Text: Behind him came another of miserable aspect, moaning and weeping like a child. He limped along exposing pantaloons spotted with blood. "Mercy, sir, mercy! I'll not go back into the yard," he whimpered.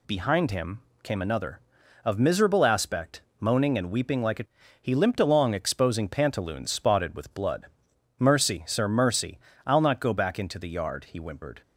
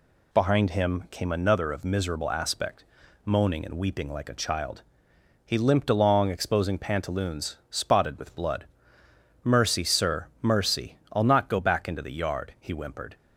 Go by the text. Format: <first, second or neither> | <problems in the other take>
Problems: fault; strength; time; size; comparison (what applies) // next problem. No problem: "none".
second | pauses between "him" and "came"; slight; at 0.8 s; 0.22 s long // skips "child"; at 4.6 s